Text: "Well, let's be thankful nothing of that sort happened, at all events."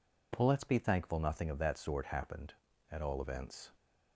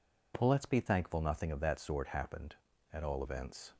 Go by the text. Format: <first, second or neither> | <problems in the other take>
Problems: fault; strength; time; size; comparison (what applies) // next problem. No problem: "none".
neither | none